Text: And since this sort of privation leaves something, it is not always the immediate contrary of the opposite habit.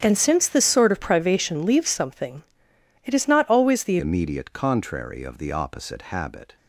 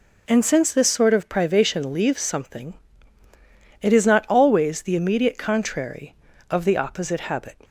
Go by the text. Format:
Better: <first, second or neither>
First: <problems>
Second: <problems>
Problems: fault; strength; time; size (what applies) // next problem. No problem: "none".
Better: second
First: starts louder than the rest; strong; until 1.0 s; 9 dB // changes voice at "immediate"; from 4.0 s on; 2.5 s long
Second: none